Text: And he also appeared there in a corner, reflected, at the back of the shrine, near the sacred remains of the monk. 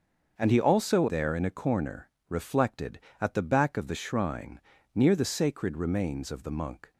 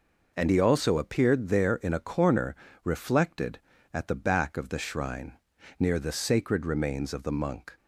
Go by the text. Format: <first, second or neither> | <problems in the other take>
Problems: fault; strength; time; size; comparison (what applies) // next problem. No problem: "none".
second | starts louder than the rest; until 1.3 s; 6.5 dB // skips "appeared"; at 1.0 s